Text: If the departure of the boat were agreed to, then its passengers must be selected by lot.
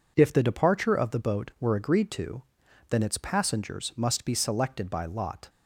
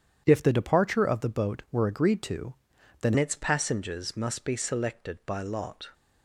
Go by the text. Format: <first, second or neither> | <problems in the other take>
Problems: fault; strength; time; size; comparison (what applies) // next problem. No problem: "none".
first | changes voice at "its"; from 3.1 s on; 2.7 s long